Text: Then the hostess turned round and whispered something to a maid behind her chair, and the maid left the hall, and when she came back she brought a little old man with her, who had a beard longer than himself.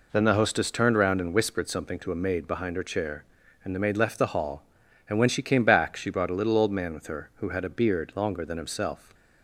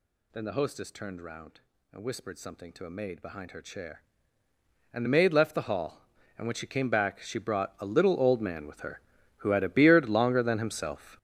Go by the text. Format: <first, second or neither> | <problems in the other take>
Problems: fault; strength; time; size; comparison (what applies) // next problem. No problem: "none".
first | gets louder; strong; throughout; 12 dB